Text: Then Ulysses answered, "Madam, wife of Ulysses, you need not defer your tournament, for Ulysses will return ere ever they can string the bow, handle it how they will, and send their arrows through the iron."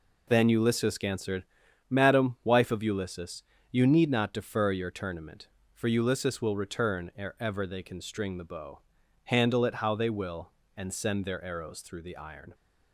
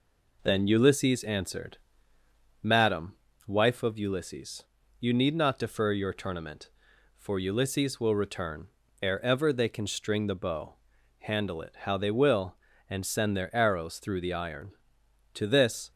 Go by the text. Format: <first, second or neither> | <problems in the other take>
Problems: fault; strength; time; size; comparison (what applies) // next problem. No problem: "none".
first | pauses between "return" and "ere"; slight; at 8.6 s; 0.34 s long // goes on to say "To this"; from 15.3 s on; 0.56 s long